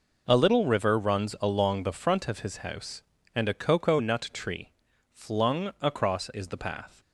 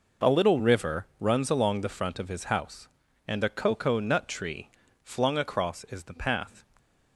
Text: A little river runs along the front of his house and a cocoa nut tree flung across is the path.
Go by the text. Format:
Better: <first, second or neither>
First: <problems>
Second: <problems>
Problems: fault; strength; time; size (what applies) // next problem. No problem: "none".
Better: neither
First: pauses between "tree" and "flung"; at 4.7 s; 0.40 s long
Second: pauses between "tree" and "flung"; slight; at 4.6 s; 0.34 s long